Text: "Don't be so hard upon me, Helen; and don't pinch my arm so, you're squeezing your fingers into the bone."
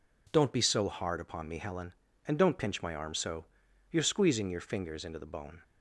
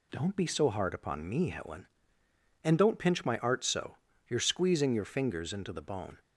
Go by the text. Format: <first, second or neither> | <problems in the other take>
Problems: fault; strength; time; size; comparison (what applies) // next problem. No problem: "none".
first | says "art" for "arm"; at 3.3 s